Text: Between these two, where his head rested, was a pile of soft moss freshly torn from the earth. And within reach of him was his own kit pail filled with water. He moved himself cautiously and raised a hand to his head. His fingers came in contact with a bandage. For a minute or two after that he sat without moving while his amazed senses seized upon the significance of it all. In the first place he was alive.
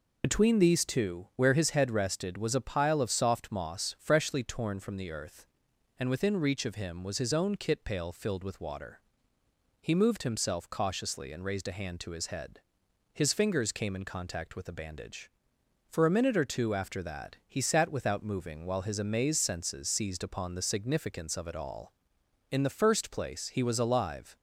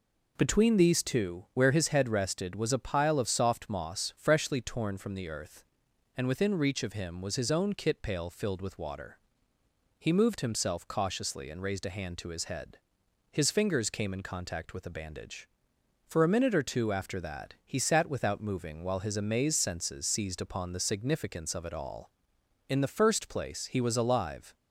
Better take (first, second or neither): second